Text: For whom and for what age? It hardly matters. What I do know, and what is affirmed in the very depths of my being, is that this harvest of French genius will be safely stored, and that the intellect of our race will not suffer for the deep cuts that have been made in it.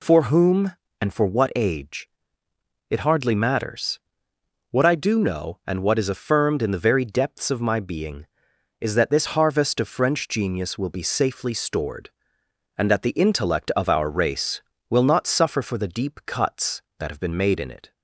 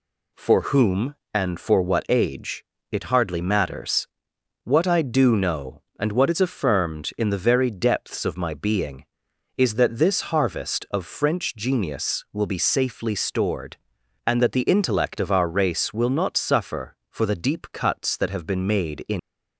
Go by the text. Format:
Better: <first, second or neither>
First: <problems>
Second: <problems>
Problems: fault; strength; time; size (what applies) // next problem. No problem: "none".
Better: first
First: none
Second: stops before "it"; at 19.1 s